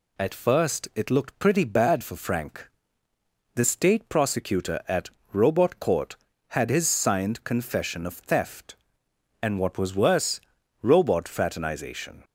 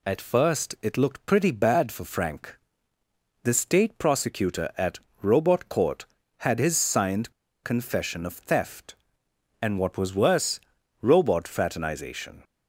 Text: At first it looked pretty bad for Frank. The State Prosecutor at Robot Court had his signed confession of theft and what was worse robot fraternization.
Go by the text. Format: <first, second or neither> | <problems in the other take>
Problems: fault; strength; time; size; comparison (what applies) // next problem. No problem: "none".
first | pauses between "at" and "Robot"; slight; at 4.9 s; 0.22 s long; slight in the first // pauses between "signed" and "confession"; slight; at 7.3 s; 0.30 s long // pauses between "worse" and "robot"; at 10.5 s; 0.42 s long; also in the first